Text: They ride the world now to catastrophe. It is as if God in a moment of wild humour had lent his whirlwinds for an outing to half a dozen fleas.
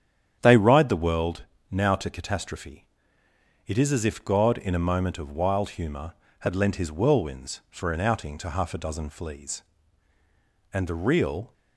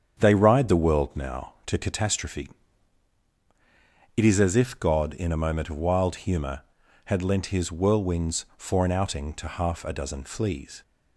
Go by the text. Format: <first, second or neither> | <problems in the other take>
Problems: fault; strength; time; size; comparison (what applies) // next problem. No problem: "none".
second | starts louder than the rest; strong; until 1.4 s; 9 dB; strong in the second // pauses between "world" and "now"; slight; at 1.4 s; 0.26 s long // goes on to say "And the real"; noticeable; from 10.7 s on; 0.80 s long